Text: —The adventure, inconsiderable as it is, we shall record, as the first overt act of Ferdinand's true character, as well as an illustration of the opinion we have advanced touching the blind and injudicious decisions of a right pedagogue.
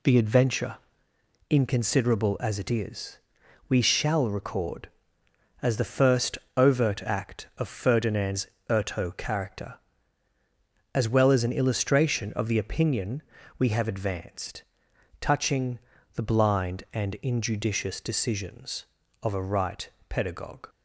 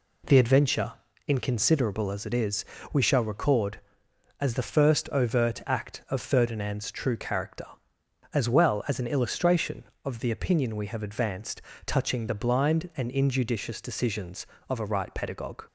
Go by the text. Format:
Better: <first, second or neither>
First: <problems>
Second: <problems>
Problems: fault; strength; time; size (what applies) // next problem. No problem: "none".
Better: second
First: pauses between "first" and "overt"; slight; at 6.3 s; 0.18 s long // says "erto" for "true"; at 8.7 s // pauses between "opinion" and "we"; at 13.2 s; 0.38 s long // pauses between "advanced" and "touching"; noticeable; at 14.6 s; 0.58 s long // pauses between "touching" and "the"; slight; at 15.7 s; 0.36 s long // pauses between "right" and "pedagogue"; slight; at 19.8 s; 0.18 s long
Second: pauses between "advanced" and "touching"; slight; at 11.6 s; 0.24 s long